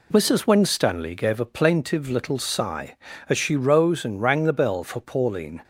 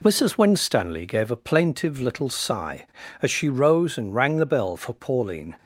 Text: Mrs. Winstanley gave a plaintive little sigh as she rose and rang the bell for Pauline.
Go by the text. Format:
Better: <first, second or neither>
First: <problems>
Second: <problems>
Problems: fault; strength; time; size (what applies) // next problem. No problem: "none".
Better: neither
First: none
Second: none